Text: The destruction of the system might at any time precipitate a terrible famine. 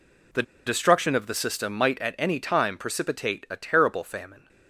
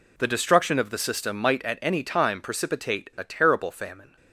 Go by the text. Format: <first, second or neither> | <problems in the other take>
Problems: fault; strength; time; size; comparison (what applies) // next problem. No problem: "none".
second | pauses between "The" and "destruction"; slight; at 0.4 s; 0.23 s long